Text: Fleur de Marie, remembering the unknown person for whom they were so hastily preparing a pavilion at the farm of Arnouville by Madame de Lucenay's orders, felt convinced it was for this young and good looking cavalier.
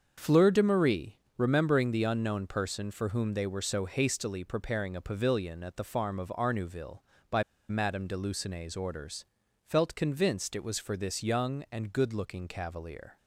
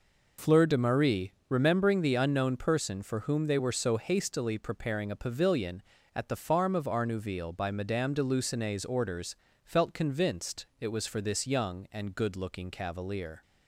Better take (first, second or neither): second